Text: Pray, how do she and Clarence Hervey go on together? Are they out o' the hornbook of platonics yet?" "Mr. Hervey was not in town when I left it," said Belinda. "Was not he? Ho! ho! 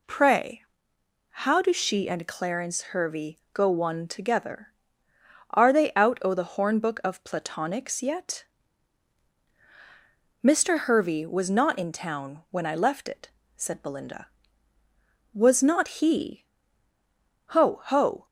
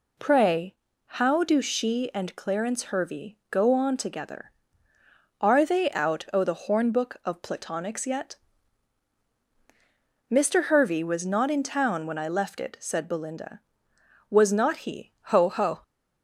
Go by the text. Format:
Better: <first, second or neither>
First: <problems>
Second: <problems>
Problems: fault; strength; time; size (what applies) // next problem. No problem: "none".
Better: second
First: pauses between "Hervey" and "go"; slight; at 3.3 s; 0.16 s long // says "one" for "on"; at 3.6 s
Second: none